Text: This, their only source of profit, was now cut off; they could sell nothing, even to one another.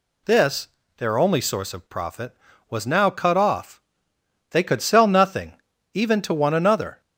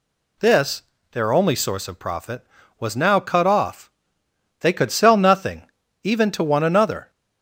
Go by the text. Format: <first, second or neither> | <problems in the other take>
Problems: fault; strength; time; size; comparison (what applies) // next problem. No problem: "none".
neither | none